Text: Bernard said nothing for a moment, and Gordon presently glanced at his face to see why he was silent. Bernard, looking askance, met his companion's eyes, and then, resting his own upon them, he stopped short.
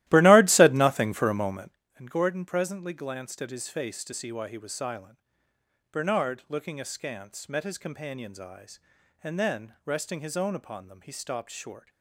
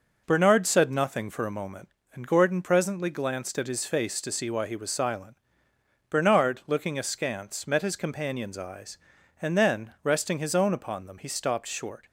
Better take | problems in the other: second | starts louder than the rest; strong; until 1.8 s; 15.5 dB

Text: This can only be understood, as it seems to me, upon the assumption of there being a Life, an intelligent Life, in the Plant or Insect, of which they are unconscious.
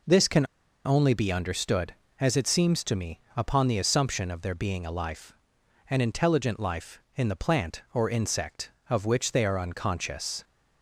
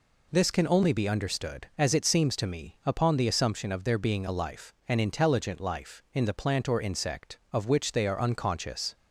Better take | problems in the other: second | pauses between "can" and "only"; at 0.4 s; 0.40 s long

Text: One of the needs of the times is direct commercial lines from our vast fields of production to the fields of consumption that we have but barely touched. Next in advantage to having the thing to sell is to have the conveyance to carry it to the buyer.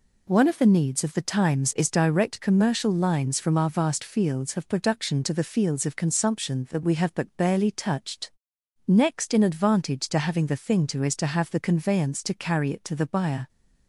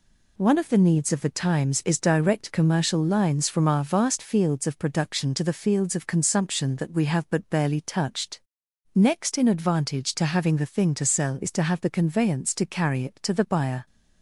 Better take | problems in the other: second | skips "sell"; at 11.0 s

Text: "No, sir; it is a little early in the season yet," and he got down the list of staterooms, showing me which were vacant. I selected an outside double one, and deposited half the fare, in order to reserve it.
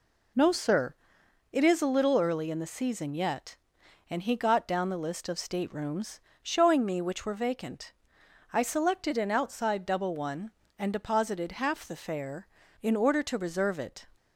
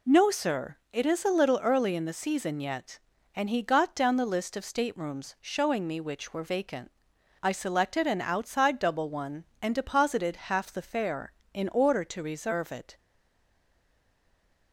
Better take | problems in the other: first | stays silent after the last word; noticeable; from 12.9 s on; 1.8 s long

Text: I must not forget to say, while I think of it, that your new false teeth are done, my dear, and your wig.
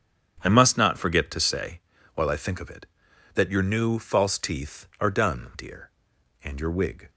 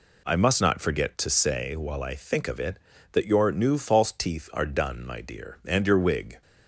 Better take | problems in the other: second | starts louder than the rest; strong; until 1.4 s; 8.5 dB // skips "my"; at 5.5 s

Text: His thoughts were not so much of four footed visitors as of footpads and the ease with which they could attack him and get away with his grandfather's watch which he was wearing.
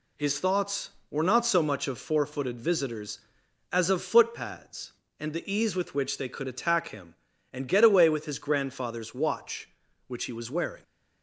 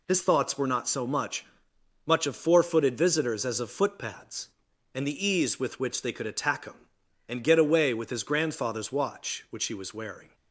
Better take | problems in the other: first | says "much" twice; at 2.0 s

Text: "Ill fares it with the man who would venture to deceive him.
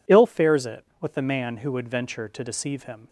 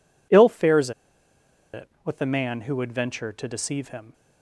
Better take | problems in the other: first | pauses between "fares" and "it"; noticeable; at 0.9 s; 0.83 s long

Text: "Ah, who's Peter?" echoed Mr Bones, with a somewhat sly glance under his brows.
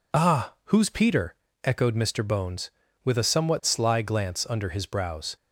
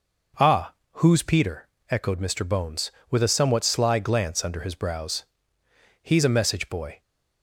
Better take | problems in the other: first | goes on to say "He's a message boy"; noticeable; from 6.0 s on; 0.98 s long

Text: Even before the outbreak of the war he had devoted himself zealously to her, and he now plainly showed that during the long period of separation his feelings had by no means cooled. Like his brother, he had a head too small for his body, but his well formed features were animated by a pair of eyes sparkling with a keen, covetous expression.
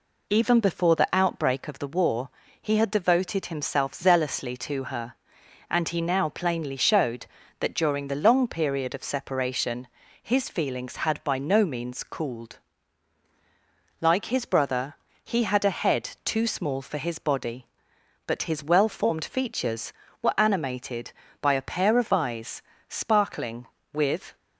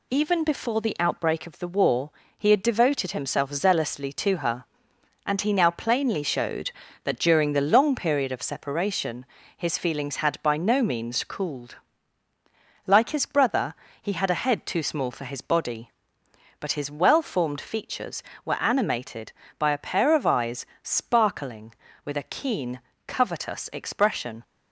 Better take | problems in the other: second | pauses between "war" and "he"; slight; at 2.2 s; 0.30 s long; slight in the second // pauses between "separation" and "his"; slight; at 9.8 s; 0.34 s long; slight in the second // pauses between "eyes" and "sparkling"; slight; at 22.6 s; 0.26 s long; slight in the second // stops before "a keen covetous expression"; at 24.3 s

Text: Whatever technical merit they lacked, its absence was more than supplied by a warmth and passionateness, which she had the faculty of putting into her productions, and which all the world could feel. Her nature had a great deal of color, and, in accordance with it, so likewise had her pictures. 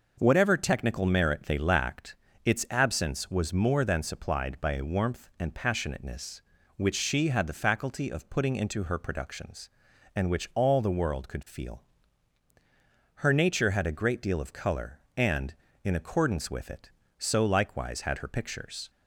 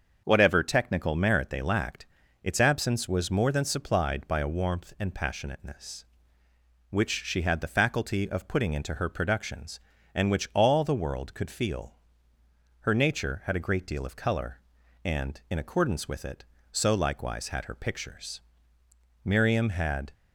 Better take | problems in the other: first | starts louder than the rest; until 1.2 s; 6.5 dB // goes on to say "Miriam had"; noticeable; from 19.2 s on; 0.88 s long

